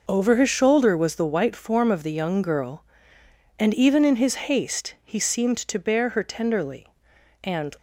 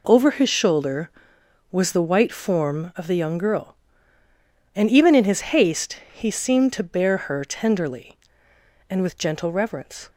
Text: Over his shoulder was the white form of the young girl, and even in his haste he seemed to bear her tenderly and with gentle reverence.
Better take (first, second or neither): second